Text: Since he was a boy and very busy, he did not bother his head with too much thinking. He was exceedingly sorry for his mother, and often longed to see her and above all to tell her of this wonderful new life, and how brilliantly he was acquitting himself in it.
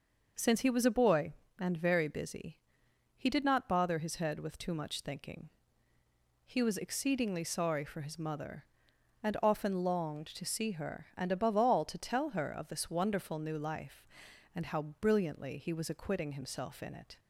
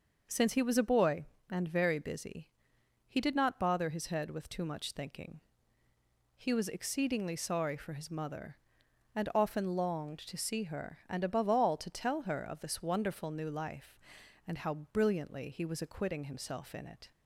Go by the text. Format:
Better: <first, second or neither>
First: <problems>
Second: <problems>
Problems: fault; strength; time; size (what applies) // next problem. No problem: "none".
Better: neither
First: pauses between "how" and "brilliantly"; slight; at 14.8 s; 0.18 s long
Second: pauses between "how" and "brilliantly"; slight; at 14.7 s; 0.18 s long